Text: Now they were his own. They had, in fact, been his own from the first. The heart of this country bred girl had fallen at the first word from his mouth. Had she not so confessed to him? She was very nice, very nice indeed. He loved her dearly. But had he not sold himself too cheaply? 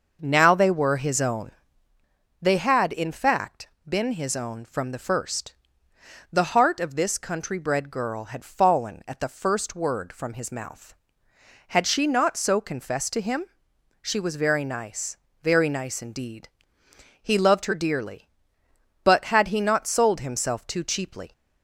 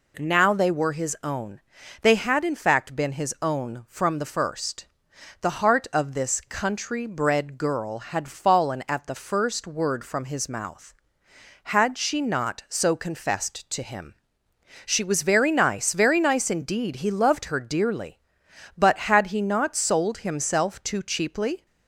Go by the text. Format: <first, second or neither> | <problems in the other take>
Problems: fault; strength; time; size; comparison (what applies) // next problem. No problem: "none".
second | starts louder than the rest; noticeable; until 2.0 s; 6 dB